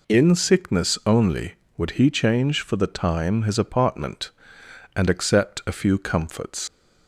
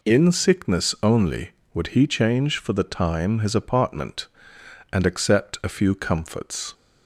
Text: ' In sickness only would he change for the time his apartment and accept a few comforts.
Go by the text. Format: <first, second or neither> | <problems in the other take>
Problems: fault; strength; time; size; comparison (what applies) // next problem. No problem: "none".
second | leaves "comforts" unfinished; at 6.6 s; 90 ms